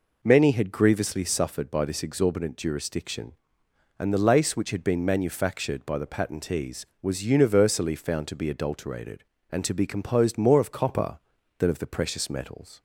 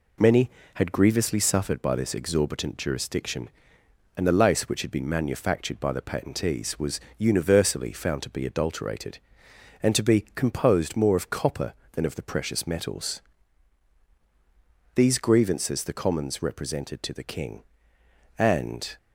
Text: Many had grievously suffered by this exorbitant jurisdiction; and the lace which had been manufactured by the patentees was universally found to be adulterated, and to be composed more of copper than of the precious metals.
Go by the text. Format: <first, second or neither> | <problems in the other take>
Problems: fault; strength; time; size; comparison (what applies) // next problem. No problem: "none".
first | pauses between "was" and "universally"; slight; at 6.9 s; 0.18 s long // goes on to say "These grievances the commons represented to the king and"; strong; from 14.9 s on; 4.0 s long